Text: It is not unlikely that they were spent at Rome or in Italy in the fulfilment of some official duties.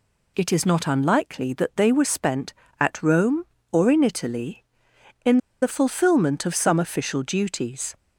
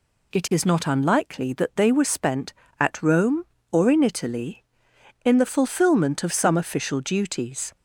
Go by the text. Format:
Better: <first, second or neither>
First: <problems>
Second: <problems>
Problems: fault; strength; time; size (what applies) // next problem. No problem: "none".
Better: second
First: pauses between "in" and "the"; slight; at 5.3 s; 0.24 s long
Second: none